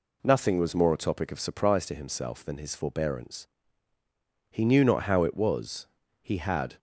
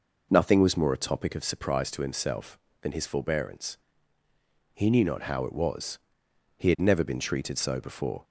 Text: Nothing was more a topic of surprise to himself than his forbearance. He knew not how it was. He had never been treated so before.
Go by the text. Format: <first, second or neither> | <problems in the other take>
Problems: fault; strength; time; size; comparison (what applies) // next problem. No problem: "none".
second | stops before "never been treated so before"; at 6.7 s